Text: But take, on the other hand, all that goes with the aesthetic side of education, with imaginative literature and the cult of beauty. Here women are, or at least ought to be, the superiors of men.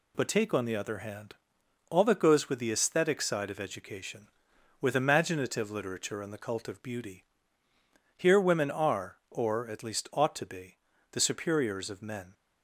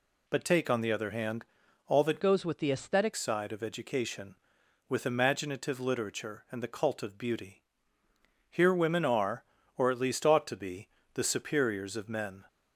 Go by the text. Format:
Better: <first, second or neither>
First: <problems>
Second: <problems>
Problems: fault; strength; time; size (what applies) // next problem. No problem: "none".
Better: first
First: none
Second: changes voice from "goes" to "aesthetic"; from 2.2 to 3.1 s; 0.9 s long